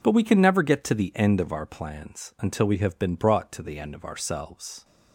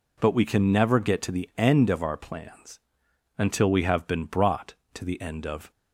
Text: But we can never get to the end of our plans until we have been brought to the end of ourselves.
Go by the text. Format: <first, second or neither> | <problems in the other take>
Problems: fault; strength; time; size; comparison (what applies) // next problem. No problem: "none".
first | pauses between "plans" and "until"; noticeable; at 2.7 s; 0.58 s long // stops before "ourselves"; at 5.7 s